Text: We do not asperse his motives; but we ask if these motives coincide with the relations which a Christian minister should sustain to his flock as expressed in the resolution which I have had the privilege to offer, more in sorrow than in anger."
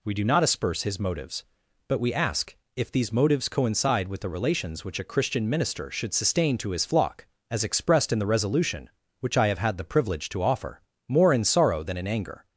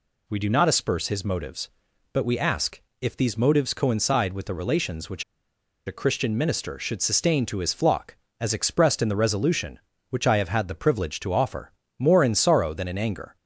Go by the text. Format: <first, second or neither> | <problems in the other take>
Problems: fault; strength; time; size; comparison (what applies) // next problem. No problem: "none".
first | pauses between "ask" and "if"; slight; at 2.8 s; 0.20 s long; slight in the first // pauses between "which" and "a"; noticeable; at 5.2 s; 0.63 s long